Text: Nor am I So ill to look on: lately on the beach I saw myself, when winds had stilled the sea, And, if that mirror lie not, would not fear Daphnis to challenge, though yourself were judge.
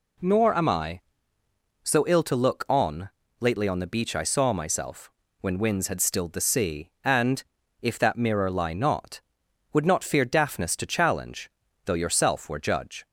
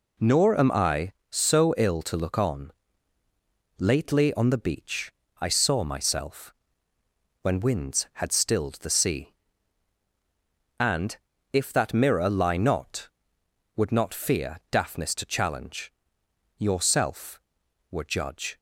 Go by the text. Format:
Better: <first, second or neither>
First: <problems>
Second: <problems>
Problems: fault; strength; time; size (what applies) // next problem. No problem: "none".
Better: first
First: none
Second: pauses between "beach" and "I"; slight; at 5.1 s; 0.30 s long // skips "though"; at 16.2 s